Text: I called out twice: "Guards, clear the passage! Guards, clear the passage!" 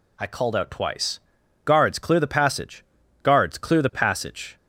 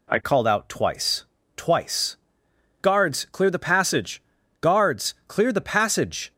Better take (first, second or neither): first